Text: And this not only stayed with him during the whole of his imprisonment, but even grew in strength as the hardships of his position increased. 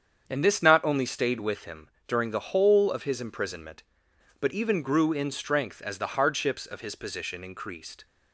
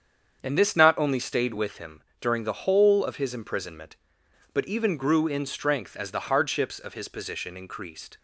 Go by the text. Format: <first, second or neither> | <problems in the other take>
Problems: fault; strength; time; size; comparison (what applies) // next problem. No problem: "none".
neither | starts louder than the rest; strong; the same in both // pauses between "him" and "during"; slight; the same in both